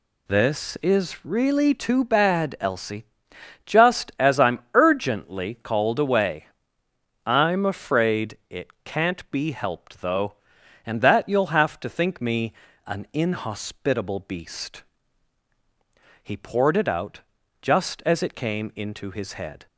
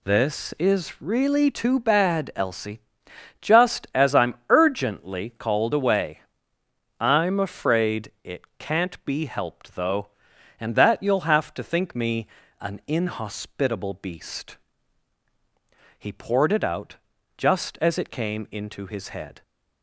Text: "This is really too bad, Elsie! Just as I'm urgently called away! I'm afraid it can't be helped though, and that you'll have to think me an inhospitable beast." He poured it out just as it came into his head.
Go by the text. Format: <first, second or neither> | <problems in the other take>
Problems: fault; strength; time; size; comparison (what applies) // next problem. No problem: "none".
neither | pauses between "I'm" and "urgently"; slight; the same in both // pauses between "it" and "can't"; slight; the same in both // pauses between "me" and "an"; slight; the same in both // pauses between "out" and "just"; the same in both